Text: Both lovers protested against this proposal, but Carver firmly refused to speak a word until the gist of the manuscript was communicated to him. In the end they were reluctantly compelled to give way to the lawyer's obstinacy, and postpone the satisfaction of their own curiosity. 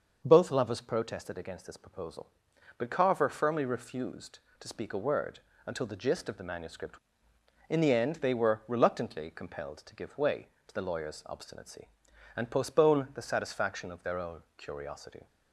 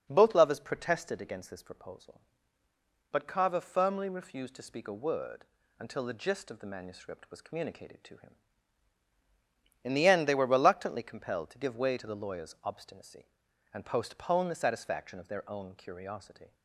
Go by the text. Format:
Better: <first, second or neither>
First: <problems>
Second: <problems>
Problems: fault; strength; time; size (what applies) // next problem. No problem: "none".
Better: second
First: starts louder than the rest; until 1.2 s; 6.5 dB // pauses between "word" and "until"; slight; at 5.4 s; 0.26 s long // skips "was communicated to him"; at 7.3 s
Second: pauses between "word" and "until"; slight; at 5.4 s; 0.34 s long